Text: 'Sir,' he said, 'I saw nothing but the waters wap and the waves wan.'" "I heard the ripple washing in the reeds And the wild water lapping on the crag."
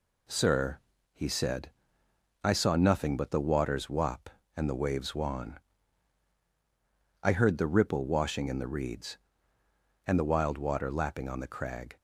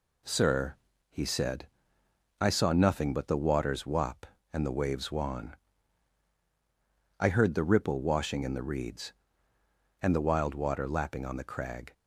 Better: neither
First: none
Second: none

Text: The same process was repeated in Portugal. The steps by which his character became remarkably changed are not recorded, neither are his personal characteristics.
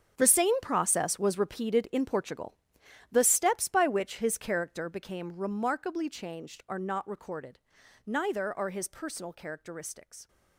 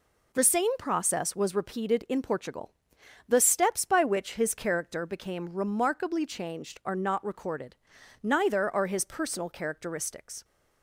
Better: second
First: gets quieter; strong; throughout; 15.5 dB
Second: none

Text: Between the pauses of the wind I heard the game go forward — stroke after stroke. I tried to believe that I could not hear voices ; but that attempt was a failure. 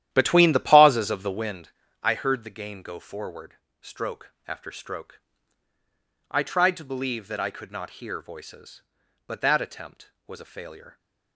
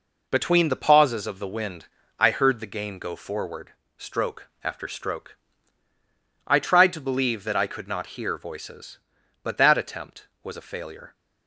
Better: second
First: starts louder than the rest; strong; until 1.7 s; 11.5 dB // pauses between "wind" and "I"; slight; at 1.6 s; 0.34 s long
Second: pauses between "wind" and "I"; slight; at 1.8 s; 0.34 s long

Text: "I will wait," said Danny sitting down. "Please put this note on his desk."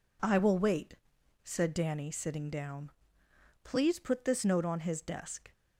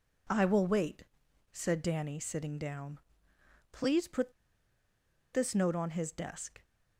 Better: first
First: none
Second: pauses between "put" and "this"; at 4.3 s; 1.0 s long

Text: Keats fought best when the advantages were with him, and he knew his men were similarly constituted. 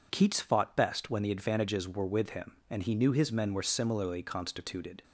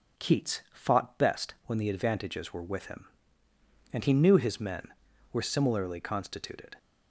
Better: neither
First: none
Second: none

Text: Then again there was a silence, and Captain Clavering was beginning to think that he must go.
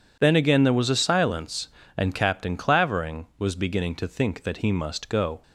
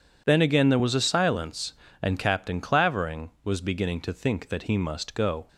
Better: neither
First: none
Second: none

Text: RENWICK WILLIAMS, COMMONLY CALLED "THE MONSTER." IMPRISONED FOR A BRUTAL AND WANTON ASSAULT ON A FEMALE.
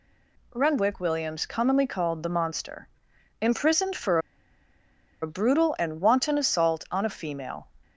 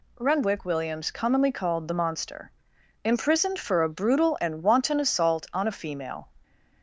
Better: second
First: pauses between "FOR" and "A"; at 4.1 s; 1.0 s long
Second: none

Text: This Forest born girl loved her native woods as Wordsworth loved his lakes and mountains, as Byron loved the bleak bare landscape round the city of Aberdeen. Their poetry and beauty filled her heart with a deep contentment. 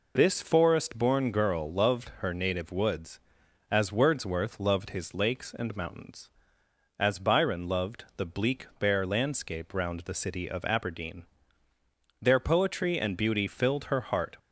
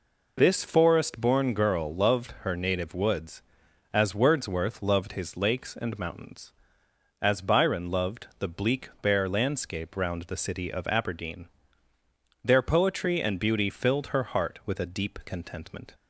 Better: second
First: stops before "with a deep contentment"; at 14.3 s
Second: none

